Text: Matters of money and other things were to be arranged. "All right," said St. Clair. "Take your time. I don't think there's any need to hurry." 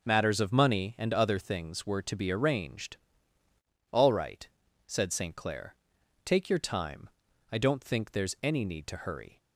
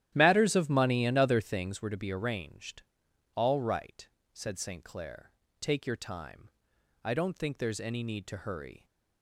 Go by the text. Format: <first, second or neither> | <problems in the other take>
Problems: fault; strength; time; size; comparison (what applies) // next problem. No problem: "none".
first | starts louder than the rest; strong; until 1.8 s; 12 dB